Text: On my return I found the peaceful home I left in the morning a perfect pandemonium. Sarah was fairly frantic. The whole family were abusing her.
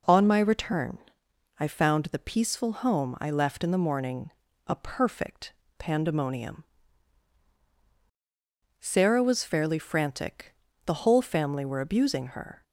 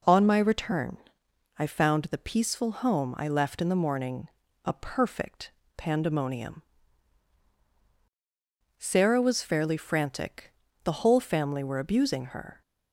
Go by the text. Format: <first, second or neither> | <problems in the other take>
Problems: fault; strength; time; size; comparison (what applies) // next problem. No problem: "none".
neither | pauses between "return" and "I"; noticeable; the same in both // pauses between "morning" and "a"; slight; the same in both // pauses between "perfect" and "pandemonium"; slight; the same in both